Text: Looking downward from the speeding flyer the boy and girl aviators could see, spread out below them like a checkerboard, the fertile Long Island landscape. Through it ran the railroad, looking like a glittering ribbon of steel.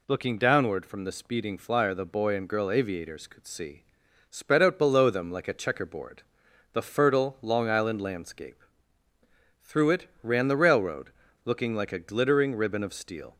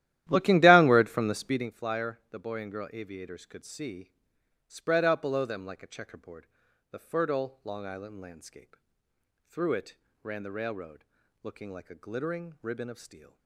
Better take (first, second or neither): first